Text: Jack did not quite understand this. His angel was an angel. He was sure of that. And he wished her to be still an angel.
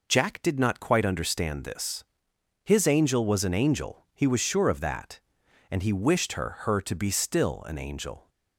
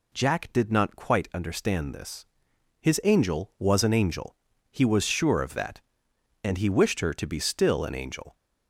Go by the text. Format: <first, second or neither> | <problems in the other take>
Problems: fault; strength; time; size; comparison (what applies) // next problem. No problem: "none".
second | says "her" twice; at 6.6 s